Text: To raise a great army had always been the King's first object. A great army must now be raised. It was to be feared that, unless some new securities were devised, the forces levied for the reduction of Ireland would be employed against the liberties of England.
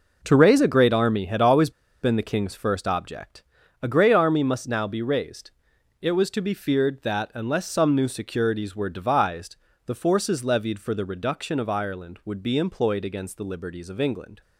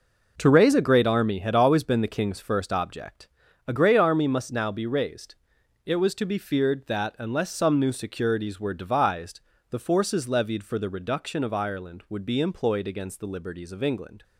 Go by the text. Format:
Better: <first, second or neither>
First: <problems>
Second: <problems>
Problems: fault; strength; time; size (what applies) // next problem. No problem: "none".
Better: second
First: pauses between "always" and "been"; slight; at 1.6 s; 0.31 s long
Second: none